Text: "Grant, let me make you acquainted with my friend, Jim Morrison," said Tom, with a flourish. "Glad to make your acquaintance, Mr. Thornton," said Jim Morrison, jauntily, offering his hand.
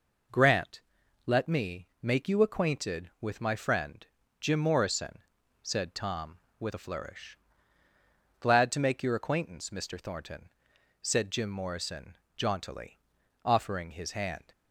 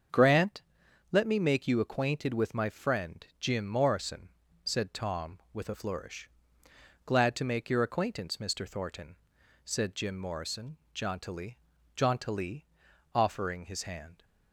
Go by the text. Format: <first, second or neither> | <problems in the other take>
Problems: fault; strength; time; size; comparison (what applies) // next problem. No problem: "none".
first | starts louder than the rest; strong; until 1.6 s; 7 dB // says "jauntily" twice; at 11.9 s